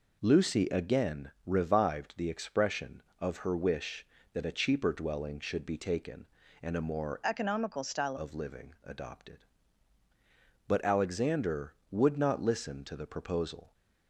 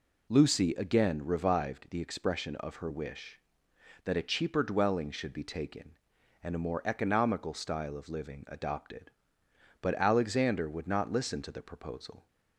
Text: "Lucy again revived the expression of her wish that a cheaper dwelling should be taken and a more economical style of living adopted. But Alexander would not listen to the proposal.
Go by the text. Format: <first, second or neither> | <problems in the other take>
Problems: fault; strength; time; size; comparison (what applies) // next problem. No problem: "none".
second | changes voice from "economical" to "style"; from 7.2 to 8.1 s; 0.9 s long